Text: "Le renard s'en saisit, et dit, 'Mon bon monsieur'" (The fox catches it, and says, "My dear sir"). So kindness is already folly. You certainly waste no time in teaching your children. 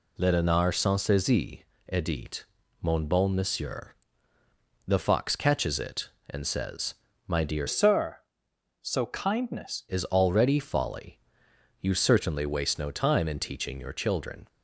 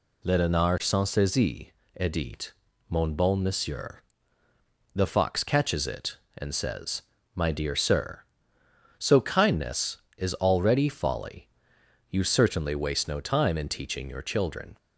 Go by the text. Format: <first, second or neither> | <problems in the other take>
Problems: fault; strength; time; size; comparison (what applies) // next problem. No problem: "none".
second | changes voice from "sir" to "kindness"; from 7.6 to 9.8 s; 2.2 s long